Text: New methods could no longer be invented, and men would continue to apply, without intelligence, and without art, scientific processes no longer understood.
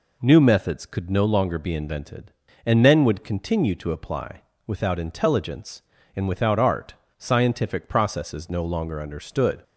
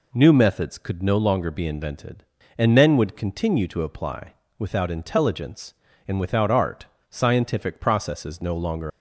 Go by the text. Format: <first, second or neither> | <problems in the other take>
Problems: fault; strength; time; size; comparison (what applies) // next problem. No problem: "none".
first | stops before "understood"; at 8.9 s